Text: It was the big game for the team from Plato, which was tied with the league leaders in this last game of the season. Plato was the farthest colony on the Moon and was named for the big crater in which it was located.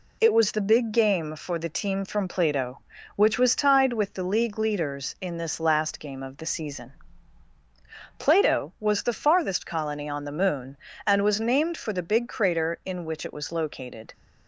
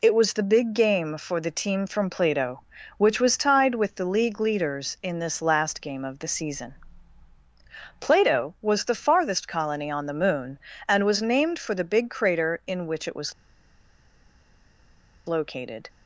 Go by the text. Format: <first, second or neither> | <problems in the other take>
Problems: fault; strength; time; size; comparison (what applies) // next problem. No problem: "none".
first | pauses between "was" and "located"; strong; at 13.3 s; 1.9 s long